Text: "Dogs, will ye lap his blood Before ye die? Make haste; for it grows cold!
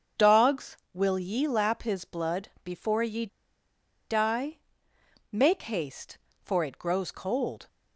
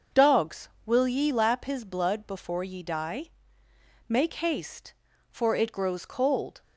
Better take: second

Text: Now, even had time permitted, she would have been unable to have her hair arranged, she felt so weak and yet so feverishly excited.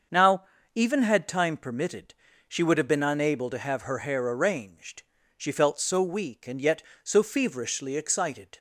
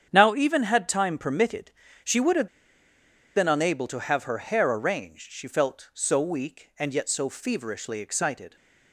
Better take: first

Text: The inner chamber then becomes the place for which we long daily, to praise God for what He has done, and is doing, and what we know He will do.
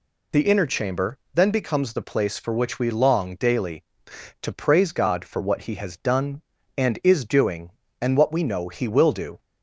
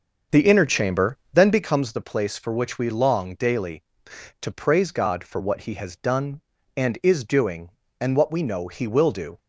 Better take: first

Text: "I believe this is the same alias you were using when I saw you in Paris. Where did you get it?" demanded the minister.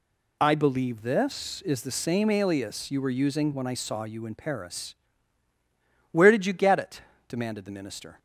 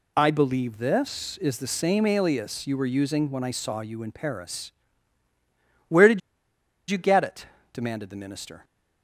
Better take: first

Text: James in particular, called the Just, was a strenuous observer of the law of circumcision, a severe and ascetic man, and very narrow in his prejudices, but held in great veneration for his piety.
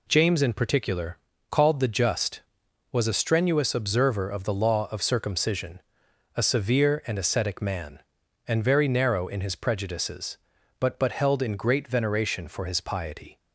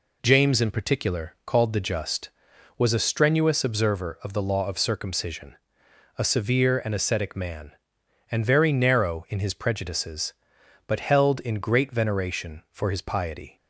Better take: second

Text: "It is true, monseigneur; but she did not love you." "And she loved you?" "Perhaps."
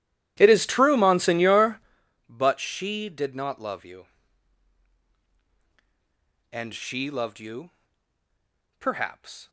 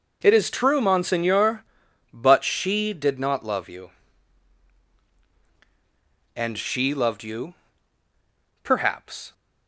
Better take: second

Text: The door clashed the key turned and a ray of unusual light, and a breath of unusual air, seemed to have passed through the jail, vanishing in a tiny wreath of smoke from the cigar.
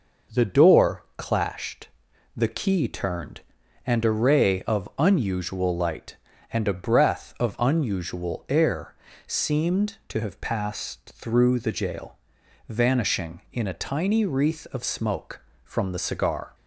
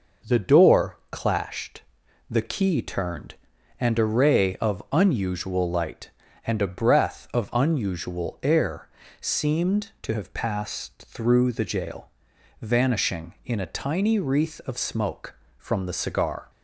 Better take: neither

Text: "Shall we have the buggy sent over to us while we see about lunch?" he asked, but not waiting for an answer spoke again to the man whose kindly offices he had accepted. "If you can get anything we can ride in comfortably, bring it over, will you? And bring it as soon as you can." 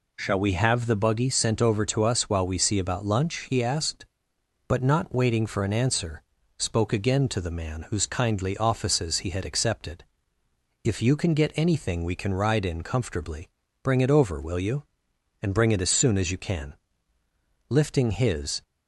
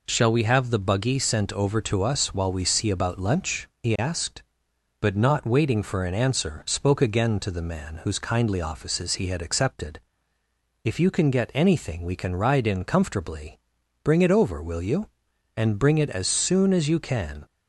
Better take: second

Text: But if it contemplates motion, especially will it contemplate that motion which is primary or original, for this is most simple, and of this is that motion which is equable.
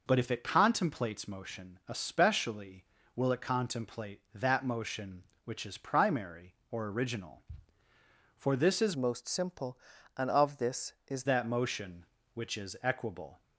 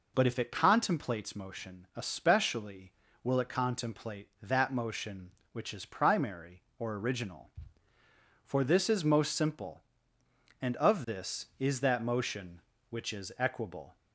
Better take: second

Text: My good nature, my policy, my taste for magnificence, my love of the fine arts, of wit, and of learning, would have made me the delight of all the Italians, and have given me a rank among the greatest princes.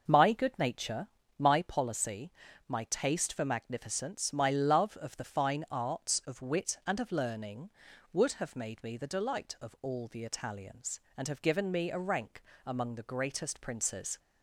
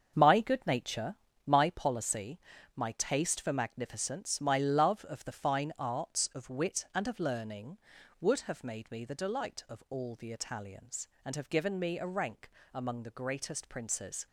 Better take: first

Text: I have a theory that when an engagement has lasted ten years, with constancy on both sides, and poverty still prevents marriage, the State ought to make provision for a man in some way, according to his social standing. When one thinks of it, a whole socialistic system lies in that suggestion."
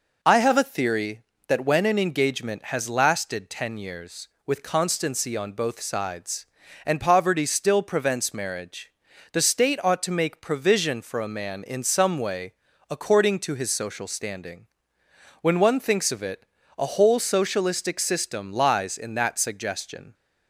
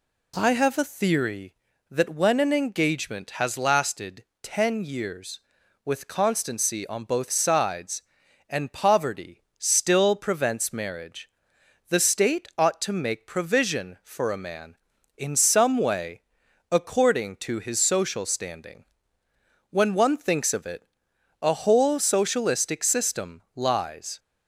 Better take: first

